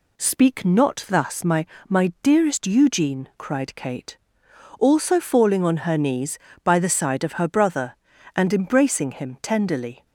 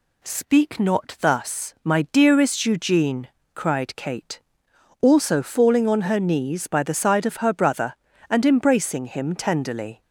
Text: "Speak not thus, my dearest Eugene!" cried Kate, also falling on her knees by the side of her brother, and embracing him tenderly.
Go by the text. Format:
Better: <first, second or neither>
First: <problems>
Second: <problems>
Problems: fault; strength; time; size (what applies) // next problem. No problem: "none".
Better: second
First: says "my" twice; at 1.8 s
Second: none